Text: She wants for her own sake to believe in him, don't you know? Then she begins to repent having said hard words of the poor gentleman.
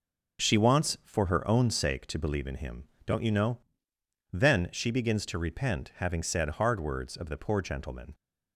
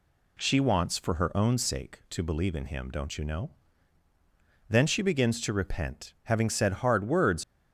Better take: first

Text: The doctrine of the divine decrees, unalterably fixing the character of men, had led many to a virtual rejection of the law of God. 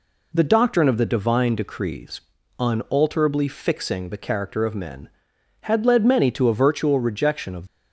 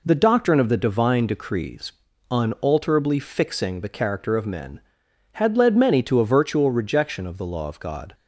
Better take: second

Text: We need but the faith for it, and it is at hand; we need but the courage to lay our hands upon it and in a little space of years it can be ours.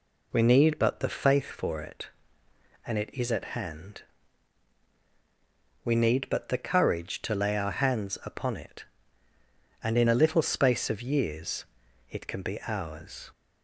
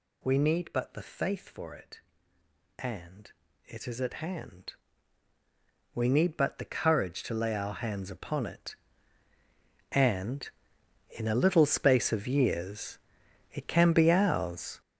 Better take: first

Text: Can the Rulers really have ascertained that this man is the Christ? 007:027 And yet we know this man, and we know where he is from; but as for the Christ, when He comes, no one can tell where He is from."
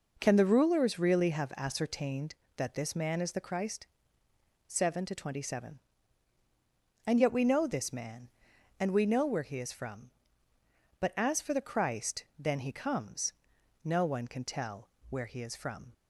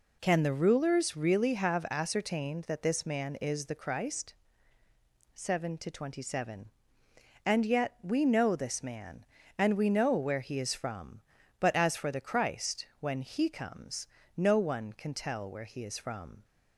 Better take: second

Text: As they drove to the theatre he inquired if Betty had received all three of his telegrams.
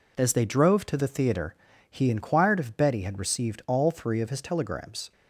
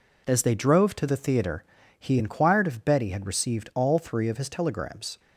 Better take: neither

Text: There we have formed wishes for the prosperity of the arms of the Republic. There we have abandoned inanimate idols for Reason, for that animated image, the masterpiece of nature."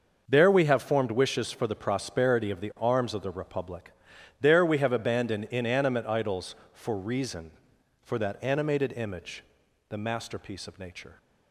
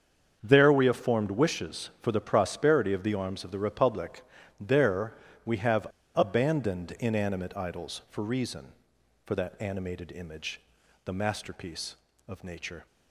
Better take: first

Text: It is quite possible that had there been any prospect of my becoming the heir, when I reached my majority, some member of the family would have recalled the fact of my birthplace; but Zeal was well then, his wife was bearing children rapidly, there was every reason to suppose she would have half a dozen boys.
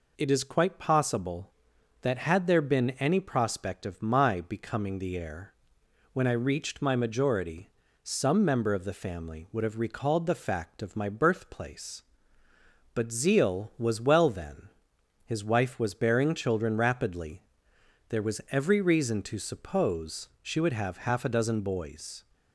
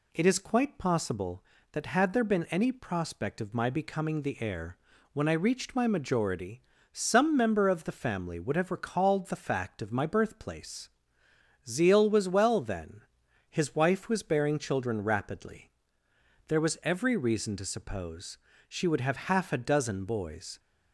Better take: first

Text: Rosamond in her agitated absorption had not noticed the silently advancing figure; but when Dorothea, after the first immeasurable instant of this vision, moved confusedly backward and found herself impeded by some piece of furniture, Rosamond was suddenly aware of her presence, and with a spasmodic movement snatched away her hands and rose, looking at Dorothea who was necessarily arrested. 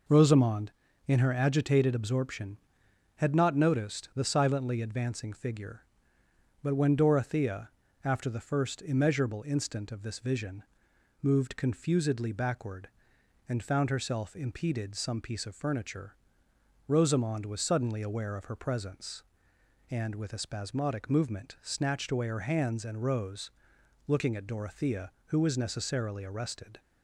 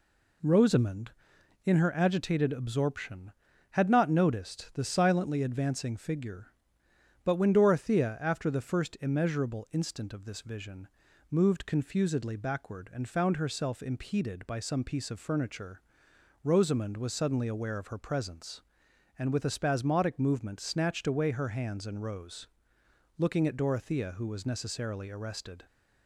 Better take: second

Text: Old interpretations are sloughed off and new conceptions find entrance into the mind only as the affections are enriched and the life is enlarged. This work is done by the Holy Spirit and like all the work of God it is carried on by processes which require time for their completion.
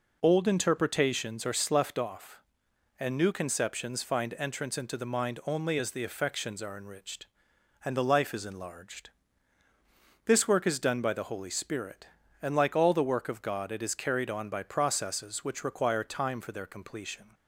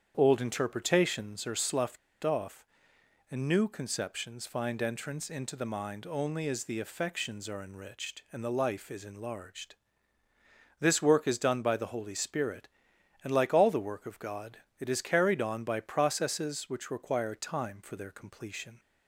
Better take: first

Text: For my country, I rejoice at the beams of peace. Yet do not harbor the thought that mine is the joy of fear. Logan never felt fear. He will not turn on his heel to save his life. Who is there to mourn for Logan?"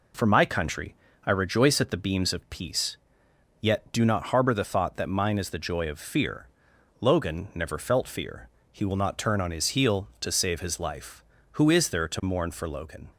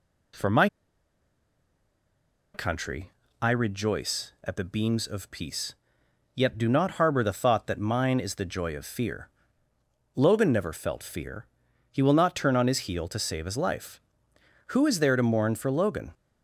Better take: first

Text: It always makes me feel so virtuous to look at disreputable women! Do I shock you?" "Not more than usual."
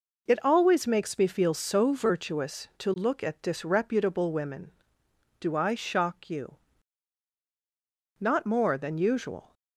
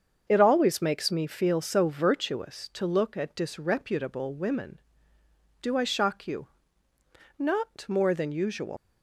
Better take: first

